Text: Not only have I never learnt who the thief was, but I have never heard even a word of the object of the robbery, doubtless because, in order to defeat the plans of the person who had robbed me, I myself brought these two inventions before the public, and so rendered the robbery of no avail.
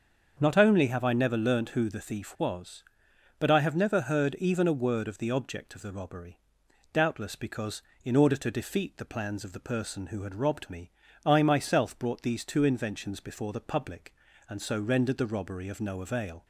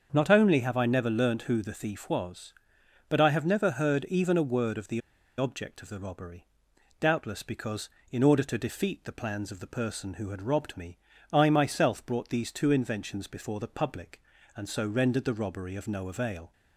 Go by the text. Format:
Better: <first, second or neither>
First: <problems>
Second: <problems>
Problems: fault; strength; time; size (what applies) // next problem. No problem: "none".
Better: first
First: starts louder than the rest; until 1.4 s; 7 dB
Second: starts louder than the rest; until 1.1 s; 7 dB // pauses between "the" and "object"; at 5.0 s; 0.37 s long